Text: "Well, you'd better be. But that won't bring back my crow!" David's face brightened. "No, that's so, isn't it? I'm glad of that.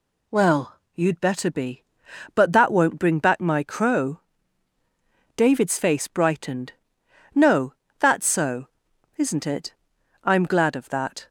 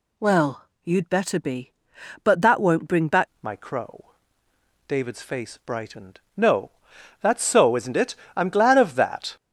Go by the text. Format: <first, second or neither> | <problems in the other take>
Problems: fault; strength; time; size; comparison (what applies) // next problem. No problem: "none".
first | changes voice at "my"; from 3.4 s on; 5.9 s long